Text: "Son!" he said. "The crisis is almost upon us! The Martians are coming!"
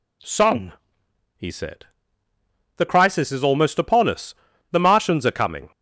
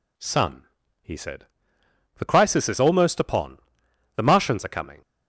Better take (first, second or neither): first